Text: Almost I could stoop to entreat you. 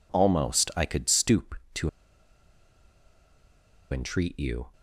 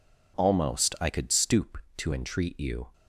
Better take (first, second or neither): second